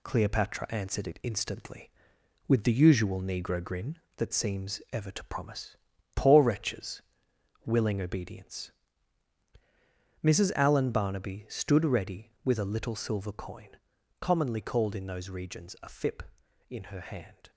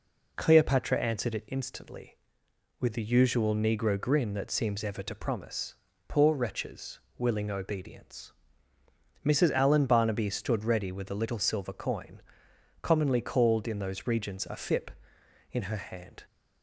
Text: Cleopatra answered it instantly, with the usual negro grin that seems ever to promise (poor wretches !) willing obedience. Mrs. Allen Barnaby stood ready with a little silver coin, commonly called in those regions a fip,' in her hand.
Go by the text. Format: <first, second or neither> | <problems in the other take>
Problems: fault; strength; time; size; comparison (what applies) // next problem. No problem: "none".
second | gets quieter; throughout; 3.5 dB